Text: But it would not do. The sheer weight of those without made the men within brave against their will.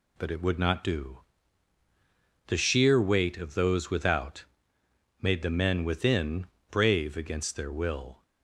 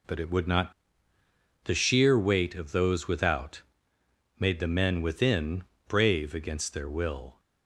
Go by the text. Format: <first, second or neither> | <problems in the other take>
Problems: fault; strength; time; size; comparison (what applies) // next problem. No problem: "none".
first | skips "do"; at 1.1 s // pauses between "without" and "made"; noticeable; at 3.6 s; 0.76 s long; noticeable in the first // pauses between "within" and "brave"; slight; at 5.6 s; 0.24 s long; slight in the first